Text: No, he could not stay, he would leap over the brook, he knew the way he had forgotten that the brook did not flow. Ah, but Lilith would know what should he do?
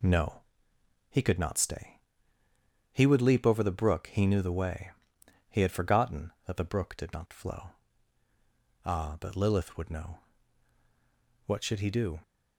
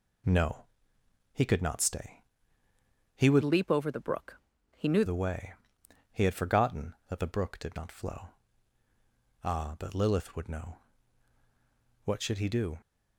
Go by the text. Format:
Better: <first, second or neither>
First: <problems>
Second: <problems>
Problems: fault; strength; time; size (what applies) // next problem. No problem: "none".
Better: first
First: pauses between "way" and "he"; noticeable; at 4.8 s; 0.58 s long // pauses between "know" and "what"; strong; at 10.1 s; 1.2 s long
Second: changes voice from "leap" to "knew"; from 3.4 to 5.0 s; 1.6 s long // pauses between "way" and "he"; noticeable; at 5.5 s; 0.58 s long // pauses between "know" and "what"; strong; at 10.7 s; 1.2 s long